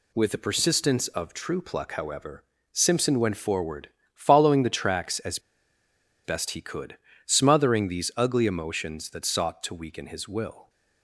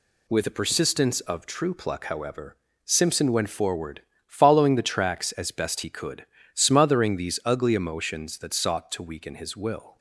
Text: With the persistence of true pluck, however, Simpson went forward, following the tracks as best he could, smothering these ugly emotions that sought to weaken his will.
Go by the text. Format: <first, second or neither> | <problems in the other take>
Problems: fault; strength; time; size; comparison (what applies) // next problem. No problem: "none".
second | pauses between "as" and "best"; noticeable; at 5.3 s; 0.85 s long